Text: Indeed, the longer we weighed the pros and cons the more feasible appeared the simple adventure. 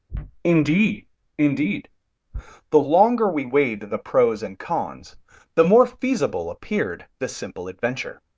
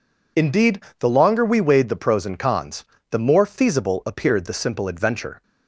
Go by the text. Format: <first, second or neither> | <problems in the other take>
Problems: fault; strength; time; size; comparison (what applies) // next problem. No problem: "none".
second | says "Indeed" twice; at 1.3 s // pauses between "cons" and "the"; at 5.1 s; 0.40 s long; slight in the second